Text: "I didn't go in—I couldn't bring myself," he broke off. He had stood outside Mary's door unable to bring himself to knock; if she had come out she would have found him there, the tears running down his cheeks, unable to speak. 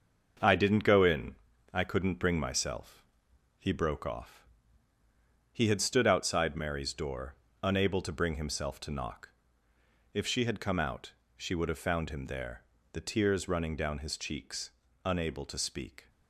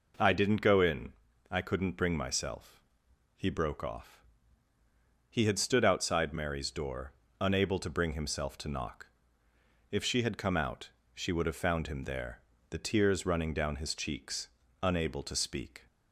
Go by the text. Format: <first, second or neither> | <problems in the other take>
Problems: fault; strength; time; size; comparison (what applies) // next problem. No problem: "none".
second | gets quieter; throughout; 6.5 dB // pauses between "door" and "unable"; slight; at 7.3 s; 0.30 s long; slight in the second // pauses between "out" and "she"; slight; at 11.1 s; 0.24 s long; slight in the second